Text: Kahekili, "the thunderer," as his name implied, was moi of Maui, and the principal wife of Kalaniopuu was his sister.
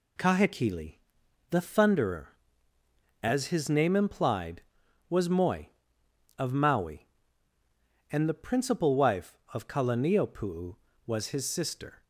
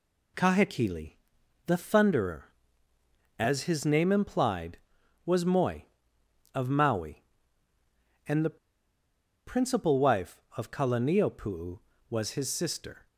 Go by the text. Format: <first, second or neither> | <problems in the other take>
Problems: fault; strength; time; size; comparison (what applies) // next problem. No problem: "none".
first | pauses between "the" and "principal"; noticeable; at 8.5 s; 0.89 s long